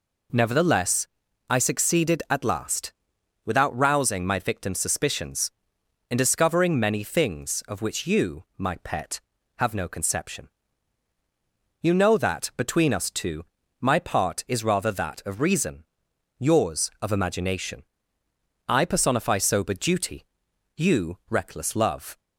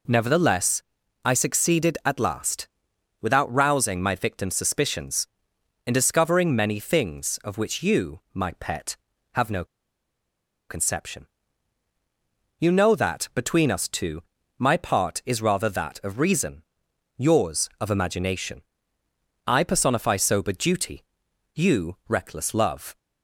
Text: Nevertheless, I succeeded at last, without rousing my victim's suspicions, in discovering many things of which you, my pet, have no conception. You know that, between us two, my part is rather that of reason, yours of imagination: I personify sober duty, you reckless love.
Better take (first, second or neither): first